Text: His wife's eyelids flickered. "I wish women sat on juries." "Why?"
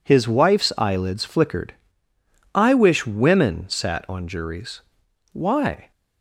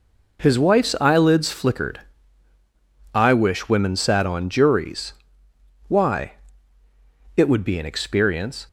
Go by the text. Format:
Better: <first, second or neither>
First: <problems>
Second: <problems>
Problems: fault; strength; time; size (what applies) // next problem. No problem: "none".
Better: first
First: none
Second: goes on to say "It would be an experience"; noticeable; from 7.3 s on; 1.3 s long